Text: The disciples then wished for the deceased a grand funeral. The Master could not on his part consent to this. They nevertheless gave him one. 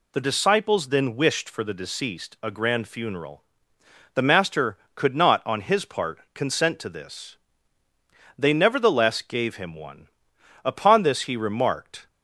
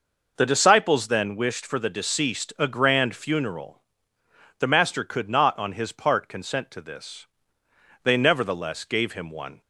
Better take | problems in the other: second | pauses between "part" and "consent"; slight; at 6.1 s; 0.16 s long // goes on to say "Upon this he remarked"; from 10.6 s on; 1.4 s long

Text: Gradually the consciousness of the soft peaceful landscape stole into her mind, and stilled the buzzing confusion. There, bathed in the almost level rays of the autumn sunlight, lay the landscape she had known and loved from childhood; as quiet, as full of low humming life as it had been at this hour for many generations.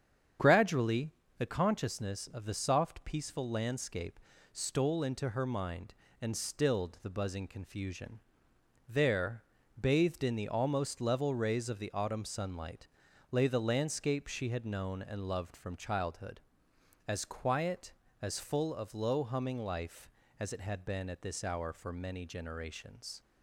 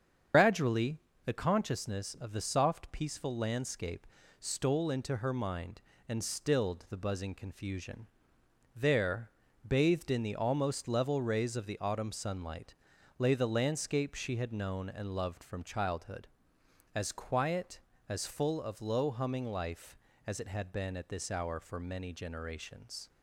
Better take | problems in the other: first | loses the start of "Gradually"; at 0.3 s; 75 ms // starts louder than the rest; strong; until 1.6 s; 7.5 dB; strong in the first // pauses between "Gradually" and "the"; slight; at 0.9 s; 0.26 s long; slight in the first // pauses between "landscape" and "stole"; slight; at 4.0 s; 0.32 s long; slight in the first

